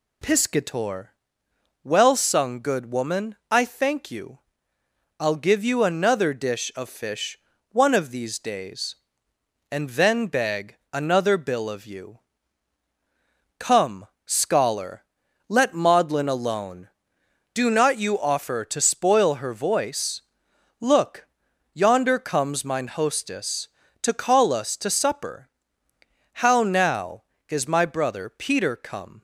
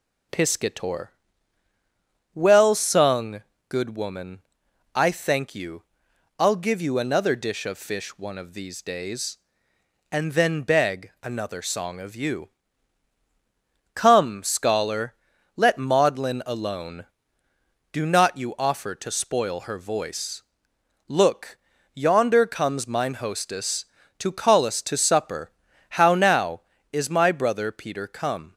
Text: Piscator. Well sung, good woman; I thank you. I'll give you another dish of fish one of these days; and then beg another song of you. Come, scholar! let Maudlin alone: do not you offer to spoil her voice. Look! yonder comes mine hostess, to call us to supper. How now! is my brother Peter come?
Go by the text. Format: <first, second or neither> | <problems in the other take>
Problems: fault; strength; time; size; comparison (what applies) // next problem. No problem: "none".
second | pauses between "fish" and "one"; slight; at 7.3 s; 0.34 s long // pauses between "beg" and "another"; slight; at 10.7 s; 0.16 s long // says "bill" for "song"; at 11.3 s